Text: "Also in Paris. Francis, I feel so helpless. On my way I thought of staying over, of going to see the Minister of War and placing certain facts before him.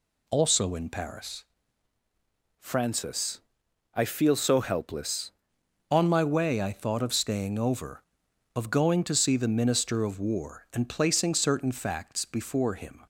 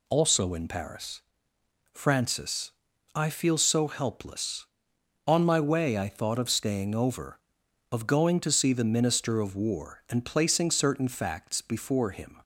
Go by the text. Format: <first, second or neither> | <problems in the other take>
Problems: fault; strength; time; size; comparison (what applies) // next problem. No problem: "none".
second | changes voice from "Francis" to "helpless"; from 2.5 to 5.3 s; 2.8 s long